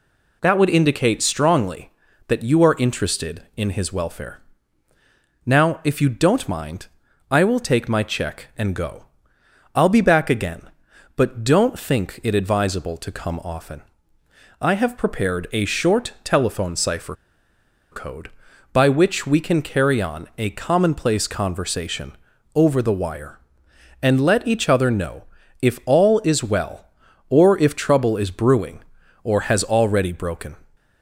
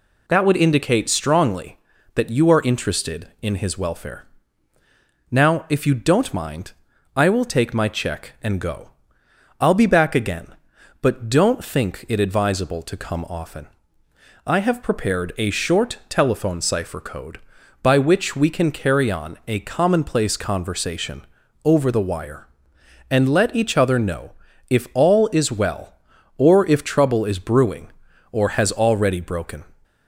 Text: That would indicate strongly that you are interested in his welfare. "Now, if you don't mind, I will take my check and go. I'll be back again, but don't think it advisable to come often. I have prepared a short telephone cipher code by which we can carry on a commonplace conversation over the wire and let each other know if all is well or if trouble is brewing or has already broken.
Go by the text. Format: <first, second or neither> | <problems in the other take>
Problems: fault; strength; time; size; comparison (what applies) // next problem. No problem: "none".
second | pauses between "cipher" and "code"; noticeable; at 17.1 s; 0.76 s long // pauses between "conversation" and "over"; at 22.1 s; 0.42 s long; also in the second // pauses between "know" and "if"; at 25.2 s; 0.38 s long; also in the second